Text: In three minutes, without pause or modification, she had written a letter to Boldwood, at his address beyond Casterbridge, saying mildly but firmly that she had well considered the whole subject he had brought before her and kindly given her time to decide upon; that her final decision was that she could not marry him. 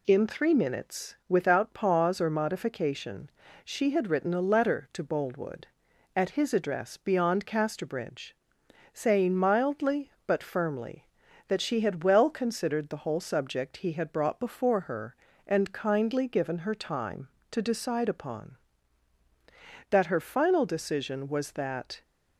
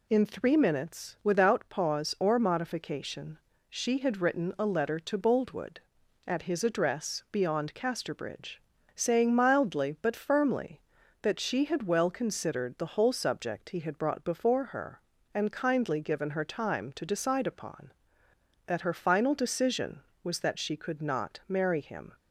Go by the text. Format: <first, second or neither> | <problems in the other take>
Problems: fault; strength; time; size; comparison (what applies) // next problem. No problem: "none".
second | stops before "she could not marry him"; at 22.0 s